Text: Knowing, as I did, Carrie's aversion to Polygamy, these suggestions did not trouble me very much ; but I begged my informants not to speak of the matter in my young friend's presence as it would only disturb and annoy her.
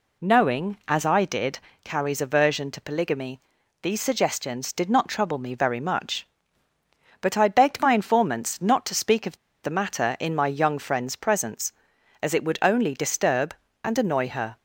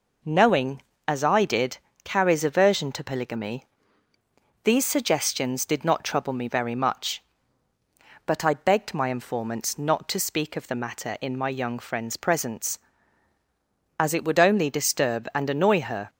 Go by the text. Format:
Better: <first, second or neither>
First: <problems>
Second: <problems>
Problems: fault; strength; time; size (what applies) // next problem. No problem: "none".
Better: second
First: pauses between "of" and "the"; slight; at 9.3 s; 0.26 s long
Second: none